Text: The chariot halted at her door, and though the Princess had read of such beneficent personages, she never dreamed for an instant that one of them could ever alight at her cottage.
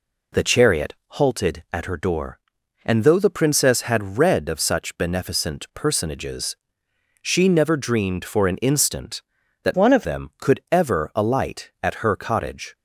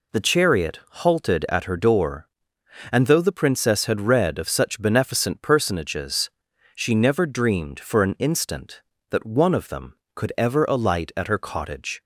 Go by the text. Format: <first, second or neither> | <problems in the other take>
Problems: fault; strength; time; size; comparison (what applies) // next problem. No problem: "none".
second | pauses between "chariot" and "halted"; slight; at 0.9 s; 0.16 s long // changes voice from "one" to "of"; from 9.7 to 10.0 s; 0.3 s long